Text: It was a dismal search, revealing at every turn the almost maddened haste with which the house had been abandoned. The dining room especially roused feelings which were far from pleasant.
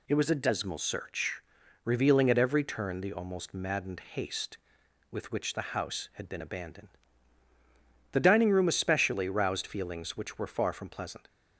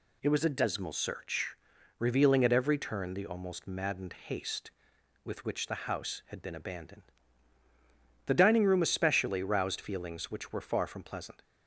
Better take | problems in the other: neither | none

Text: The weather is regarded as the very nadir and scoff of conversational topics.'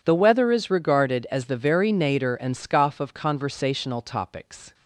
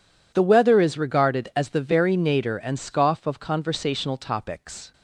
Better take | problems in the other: neither | none

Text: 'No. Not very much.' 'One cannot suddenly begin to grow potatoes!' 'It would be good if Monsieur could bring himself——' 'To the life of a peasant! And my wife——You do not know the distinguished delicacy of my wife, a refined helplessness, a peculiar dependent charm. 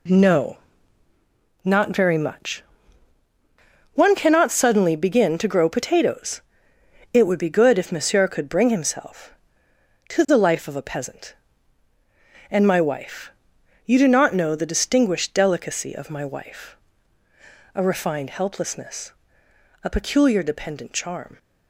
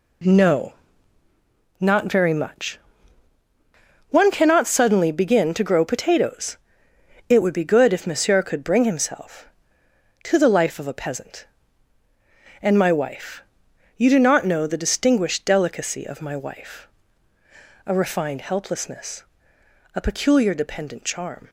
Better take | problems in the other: neither | none

